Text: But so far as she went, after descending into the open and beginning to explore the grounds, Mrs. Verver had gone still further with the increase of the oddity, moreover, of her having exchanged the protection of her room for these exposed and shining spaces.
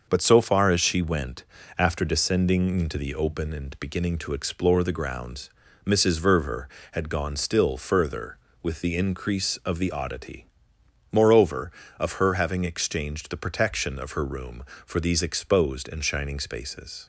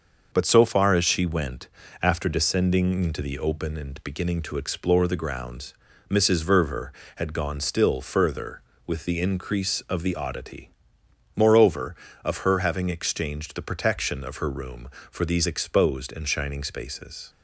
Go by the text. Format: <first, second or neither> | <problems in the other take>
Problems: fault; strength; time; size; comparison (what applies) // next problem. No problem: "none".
neither | starts louder than the rest; the same in both